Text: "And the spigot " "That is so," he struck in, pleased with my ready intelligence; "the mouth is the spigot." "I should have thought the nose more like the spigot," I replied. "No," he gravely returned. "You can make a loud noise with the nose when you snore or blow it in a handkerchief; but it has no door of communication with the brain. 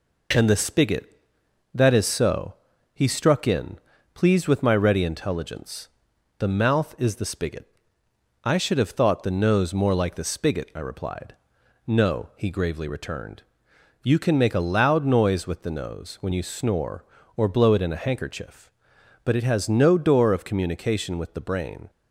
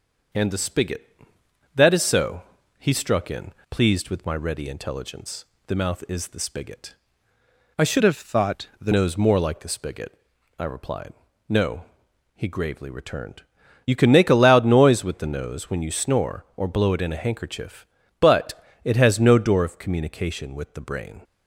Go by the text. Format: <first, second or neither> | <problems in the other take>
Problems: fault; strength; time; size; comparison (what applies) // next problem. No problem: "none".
first | changes voice from "have" to "the"; from 8.0 to 8.9 s; 0.9 s long // pauses between "but" and "it"; slight; at 18.5 s; 0.28 s long